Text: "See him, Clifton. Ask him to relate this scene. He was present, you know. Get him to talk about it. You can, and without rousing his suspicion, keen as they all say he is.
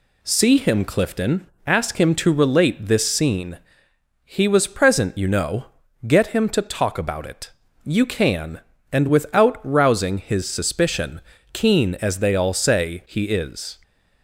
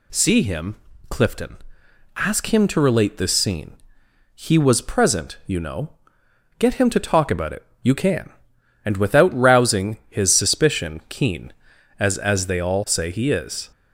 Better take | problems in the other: first | says "as" twice; at 12.1 s

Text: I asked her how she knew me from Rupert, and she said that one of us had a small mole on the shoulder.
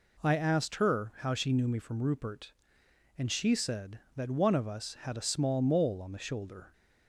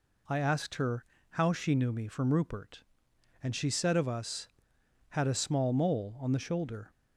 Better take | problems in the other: first | pauses between "her" and "how"; slight; at 1.0 s; 0.26 s long // skips "that one"; at 3.9 s

